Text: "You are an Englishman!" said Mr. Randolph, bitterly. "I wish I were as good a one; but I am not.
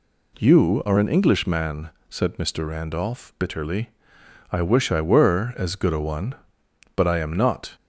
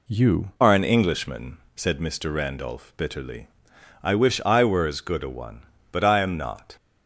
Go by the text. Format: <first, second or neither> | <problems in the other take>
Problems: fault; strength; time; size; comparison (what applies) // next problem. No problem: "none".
first | changes voice at "are"; from 0.6 s on; 6.1 s long